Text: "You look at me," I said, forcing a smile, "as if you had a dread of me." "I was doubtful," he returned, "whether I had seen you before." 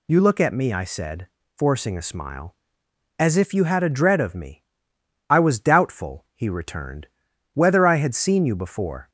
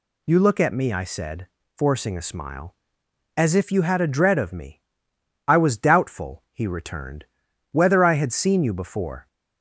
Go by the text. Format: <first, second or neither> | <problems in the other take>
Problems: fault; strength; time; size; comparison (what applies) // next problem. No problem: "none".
neither | none